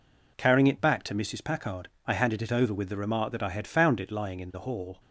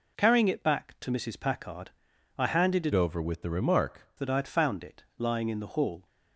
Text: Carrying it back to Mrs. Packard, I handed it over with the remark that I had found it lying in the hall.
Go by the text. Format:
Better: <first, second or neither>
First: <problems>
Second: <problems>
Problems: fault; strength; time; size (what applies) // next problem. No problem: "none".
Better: first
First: none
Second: changes voice from "over" to "remark"; from 2.9 to 4.0 s; 1.1 s long // pauses between "it" and "lying"; slight; at 5.0 s; 0.16 s long